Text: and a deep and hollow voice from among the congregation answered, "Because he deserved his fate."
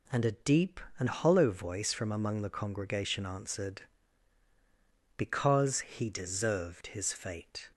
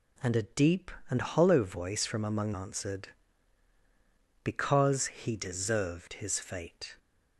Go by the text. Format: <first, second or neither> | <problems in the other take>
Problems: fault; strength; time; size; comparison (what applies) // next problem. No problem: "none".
first | skips "the congregation"; at 2.5 s